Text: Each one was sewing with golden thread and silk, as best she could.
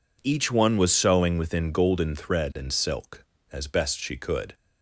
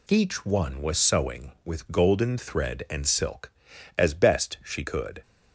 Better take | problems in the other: second | says "within" for "with"; at 1.3 s

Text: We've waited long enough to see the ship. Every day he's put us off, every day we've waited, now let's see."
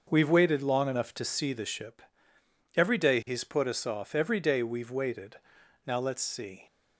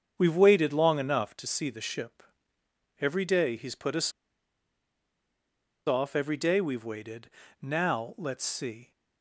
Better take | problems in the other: first | starts louder than the rest; strong; until 1.1 s; 7.5 dB; noticeable in the first // pauses between "us" and "off"; strong; at 4.1 s; 1.7 s long

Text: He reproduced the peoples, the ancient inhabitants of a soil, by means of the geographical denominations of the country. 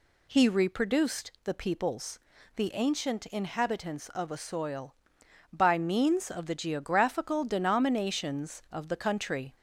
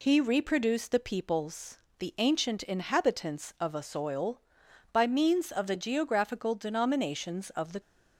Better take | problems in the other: first | stops before "country"; at 7.7 s

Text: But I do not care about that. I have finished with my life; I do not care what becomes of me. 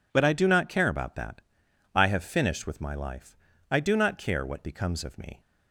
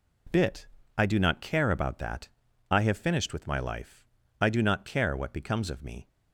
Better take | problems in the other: first | says "Bit" for "But"; at 0.3 s

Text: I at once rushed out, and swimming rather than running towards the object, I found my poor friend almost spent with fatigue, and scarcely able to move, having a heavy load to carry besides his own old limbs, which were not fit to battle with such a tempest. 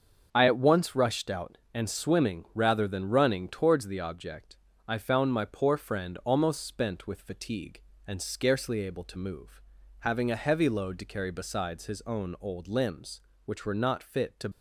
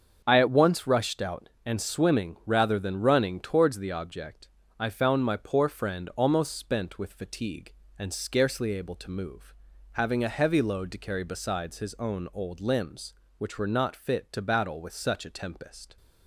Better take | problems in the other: second | starts louder than the rest; until 1.3 s; 6.5 dB; also in the second // stops before "battle with such a tempest"; at 14.5 s

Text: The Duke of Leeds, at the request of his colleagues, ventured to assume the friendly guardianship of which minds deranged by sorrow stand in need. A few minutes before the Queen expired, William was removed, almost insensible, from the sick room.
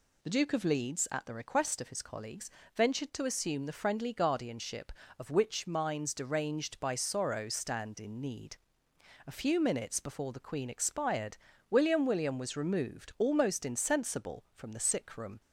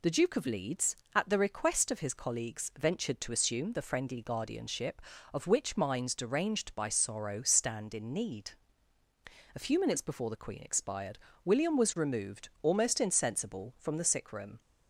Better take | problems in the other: second | says "William" twice; at 12.0 s

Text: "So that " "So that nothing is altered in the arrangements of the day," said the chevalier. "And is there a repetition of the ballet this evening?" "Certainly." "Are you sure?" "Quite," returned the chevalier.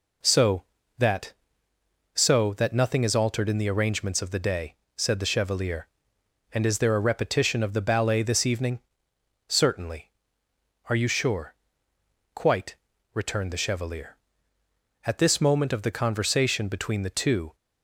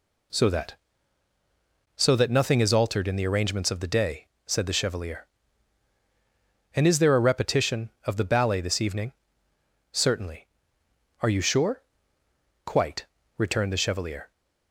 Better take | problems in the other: second | goes on to say "At this moment of the conversation between the two"; strong; from 15.0 s on; 2.4 s long

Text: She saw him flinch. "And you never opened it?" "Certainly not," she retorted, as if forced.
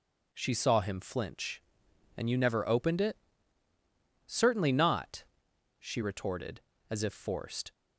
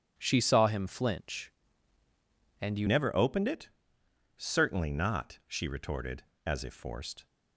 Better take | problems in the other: first | changes voice at "never"; from 2.8 s on; 4.4 s long

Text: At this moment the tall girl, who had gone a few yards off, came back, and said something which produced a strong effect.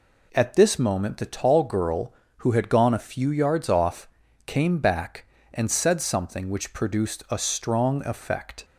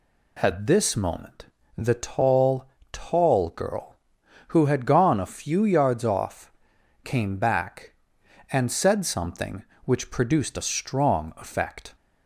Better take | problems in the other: first | pauses between "moment" and "the"; slight; at 1.4 s; 0.30 s long // says "tall" twice; at 2.9 s

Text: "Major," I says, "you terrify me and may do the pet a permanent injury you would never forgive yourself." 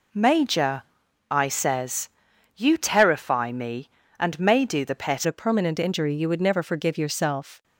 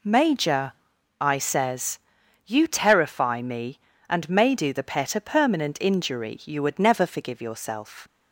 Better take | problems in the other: second | changes voice at "a"; from 5.2 s on; 2.4 s long

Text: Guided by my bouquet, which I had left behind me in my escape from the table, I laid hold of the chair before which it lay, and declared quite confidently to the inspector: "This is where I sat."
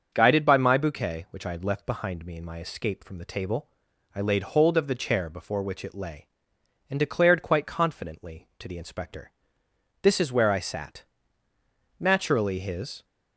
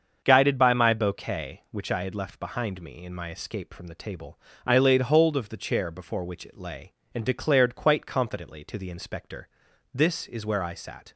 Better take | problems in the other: second | starts louder than the rest; until 1.1 s; 6.5 dB; also in the second // goes on to say "Naturally his"; noticeable; from 11.9 s on; 1.0 s long

